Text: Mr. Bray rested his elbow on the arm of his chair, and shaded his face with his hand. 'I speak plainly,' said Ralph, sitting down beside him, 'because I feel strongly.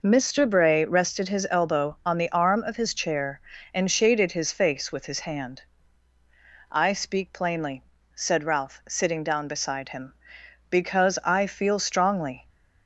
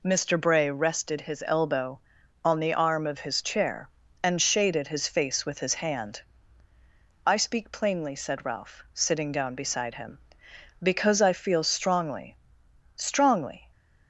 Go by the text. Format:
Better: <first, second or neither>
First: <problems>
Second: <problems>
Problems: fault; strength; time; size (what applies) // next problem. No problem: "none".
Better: first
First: none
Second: says "strongly" twice; at 12.9 s